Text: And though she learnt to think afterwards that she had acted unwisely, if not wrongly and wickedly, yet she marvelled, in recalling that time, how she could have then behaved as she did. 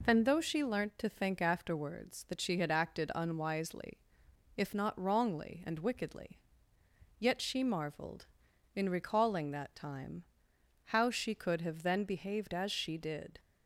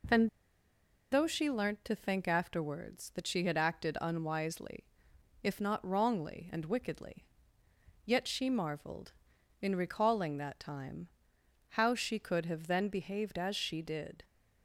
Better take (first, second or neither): first